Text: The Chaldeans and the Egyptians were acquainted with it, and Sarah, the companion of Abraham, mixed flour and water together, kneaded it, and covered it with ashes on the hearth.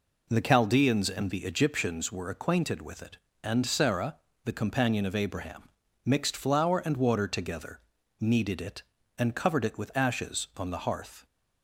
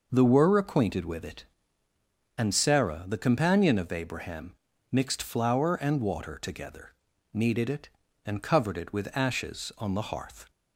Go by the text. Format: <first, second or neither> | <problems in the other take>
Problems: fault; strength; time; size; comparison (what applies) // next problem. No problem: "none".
first | skips "Chaldeans and the Egyptians"; at 0.2 s